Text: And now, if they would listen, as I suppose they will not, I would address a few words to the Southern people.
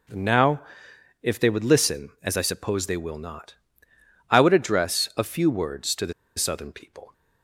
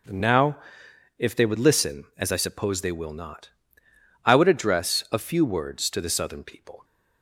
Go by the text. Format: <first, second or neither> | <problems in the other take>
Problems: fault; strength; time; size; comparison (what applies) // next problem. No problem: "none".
second | pauses between "the" and "Southern"; slight; at 6.1 s; 0.25 s long